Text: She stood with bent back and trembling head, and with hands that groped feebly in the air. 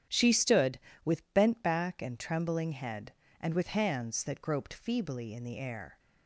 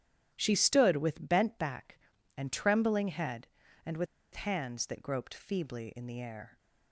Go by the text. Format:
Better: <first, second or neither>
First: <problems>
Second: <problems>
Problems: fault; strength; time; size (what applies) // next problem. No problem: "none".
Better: first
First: starts louder than the rest; strong; until 1.4 s; 9.5 dB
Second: starts louder than the rest; strong; until 1.3 s; 10.5 dB // pauses between "with" and "hands"; slight; at 4.0 s; 0.27 s long